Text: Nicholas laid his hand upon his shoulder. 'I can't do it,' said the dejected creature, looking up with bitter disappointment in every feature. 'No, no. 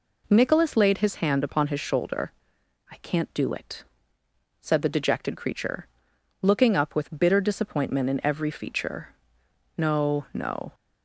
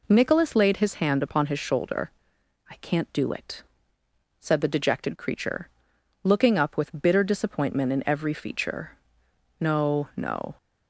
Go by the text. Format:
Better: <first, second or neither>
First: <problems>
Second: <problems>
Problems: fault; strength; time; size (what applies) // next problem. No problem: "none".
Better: neither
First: none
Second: none